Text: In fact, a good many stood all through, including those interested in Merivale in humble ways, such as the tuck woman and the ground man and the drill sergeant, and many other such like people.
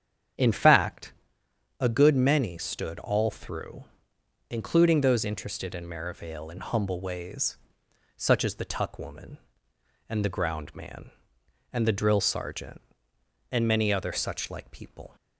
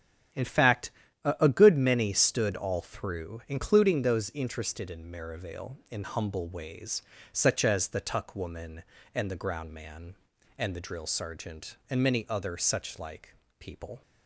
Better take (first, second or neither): first